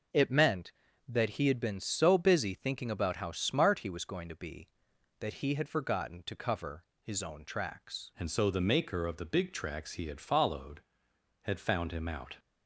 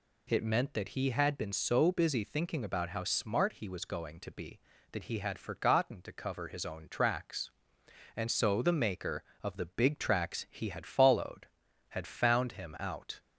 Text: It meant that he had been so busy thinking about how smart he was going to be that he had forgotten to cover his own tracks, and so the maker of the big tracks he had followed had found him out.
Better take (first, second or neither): second